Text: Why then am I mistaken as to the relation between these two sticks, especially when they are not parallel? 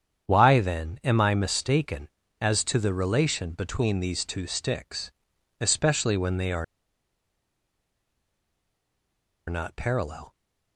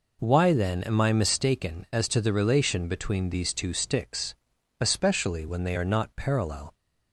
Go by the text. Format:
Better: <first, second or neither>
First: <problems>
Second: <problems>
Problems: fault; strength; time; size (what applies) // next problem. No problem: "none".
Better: second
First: starts louder than the rest; strong; until 1.3 s; 8 dB // pauses between "are" and "not"; strong; at 6.6 s; 2.8 s long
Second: none